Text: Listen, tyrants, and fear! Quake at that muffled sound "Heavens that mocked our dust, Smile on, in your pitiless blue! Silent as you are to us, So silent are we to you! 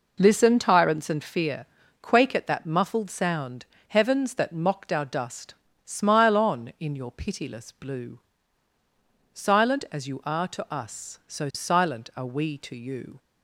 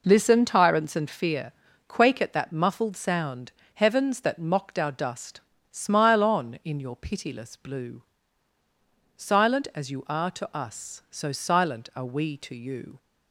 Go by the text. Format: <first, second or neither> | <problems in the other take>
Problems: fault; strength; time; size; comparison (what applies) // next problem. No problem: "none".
neither | pauses between "sound" and "Heavens"; slight; the same in both